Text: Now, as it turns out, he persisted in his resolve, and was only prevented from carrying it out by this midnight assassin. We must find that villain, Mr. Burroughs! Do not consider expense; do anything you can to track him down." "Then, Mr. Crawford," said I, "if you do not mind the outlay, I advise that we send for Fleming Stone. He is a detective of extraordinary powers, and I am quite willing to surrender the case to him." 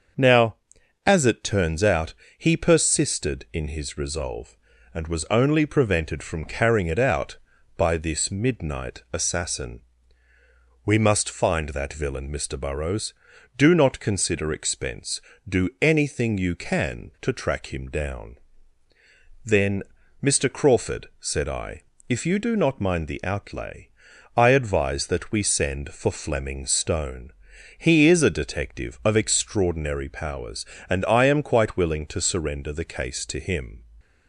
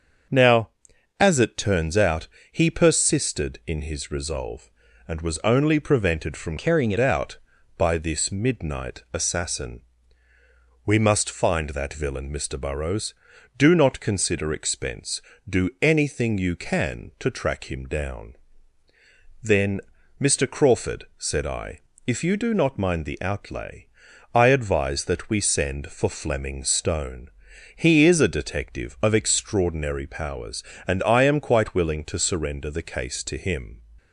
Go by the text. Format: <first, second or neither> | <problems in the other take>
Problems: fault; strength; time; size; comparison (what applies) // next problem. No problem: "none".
first | starts louder than the rest; until 1.8 s; 6.5 dB; also in the first // changes voice from "carrying" to "it"; from 6.5 to 6.9 s; 0.4 s long